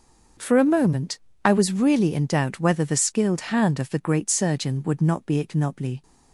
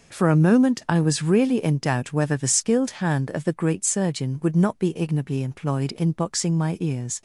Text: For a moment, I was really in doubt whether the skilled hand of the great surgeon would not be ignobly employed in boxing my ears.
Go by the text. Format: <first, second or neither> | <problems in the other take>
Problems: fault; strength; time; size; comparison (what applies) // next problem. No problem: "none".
second | starts louder than the rest; until 1.6 s; 6.5 dB // stops before "employed in boxing my ears"; at 6.0 s